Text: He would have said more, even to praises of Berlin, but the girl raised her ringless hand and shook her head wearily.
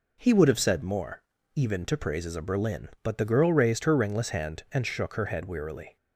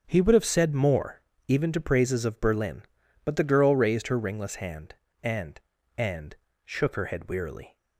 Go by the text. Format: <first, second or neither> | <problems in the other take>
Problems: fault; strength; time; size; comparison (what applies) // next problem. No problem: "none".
first | starts louder than the rest; strong; until 1.0 s; 7 dB // says "and" twice; at 5.9 s